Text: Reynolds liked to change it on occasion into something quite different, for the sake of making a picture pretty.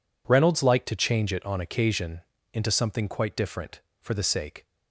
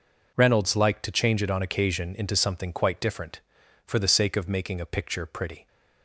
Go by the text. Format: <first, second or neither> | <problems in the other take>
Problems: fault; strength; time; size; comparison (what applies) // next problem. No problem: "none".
second | pauses between "occasion" and "into"; slight; at 2.2 s; 0.30 s long // stops before "of making a picture pretty"; at 4.6 s